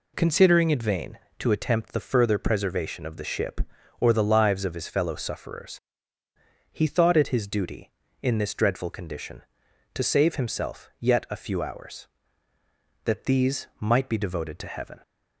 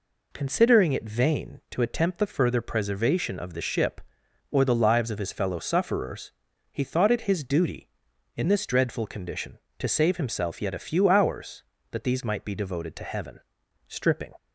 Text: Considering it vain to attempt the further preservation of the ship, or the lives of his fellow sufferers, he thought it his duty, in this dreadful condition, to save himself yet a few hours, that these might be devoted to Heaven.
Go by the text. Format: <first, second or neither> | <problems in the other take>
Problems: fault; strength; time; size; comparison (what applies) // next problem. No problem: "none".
first | goes on to say "Stripping"; slight; from 13.8 s on; 0.46 s long